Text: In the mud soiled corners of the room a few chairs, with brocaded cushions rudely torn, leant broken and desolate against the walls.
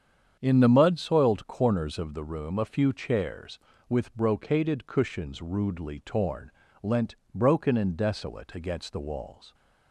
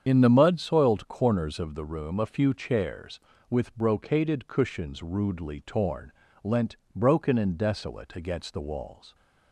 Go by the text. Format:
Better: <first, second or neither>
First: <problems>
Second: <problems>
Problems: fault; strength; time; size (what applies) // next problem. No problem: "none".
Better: first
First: starts louder than the rest; strong; until 1.4 s; 8 dB // pauses between "leant" and "broken"; slight; at 7.1 s; 0.18 s long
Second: loses the start of "In"; at 0.0 s; 60 ms // starts louder than the rest; strong; until 1.0 s; 8 dB // pauses between "leant" and "broken"; slight; at 6.7 s; 0.18 s long